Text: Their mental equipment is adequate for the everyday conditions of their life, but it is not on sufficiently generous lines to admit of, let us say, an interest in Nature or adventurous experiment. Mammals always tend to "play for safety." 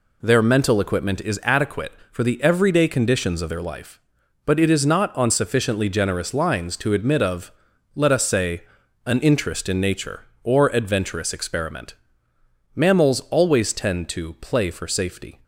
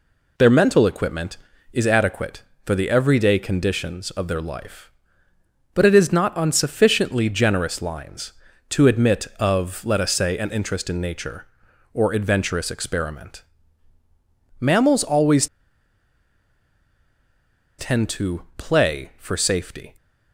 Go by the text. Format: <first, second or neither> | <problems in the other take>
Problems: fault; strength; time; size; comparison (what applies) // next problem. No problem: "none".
first | pauses between "always" and "tend"; strong; at 15.4 s; 2.3 s long